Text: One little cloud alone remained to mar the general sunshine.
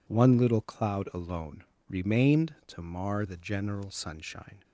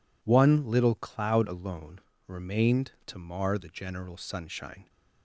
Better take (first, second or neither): neither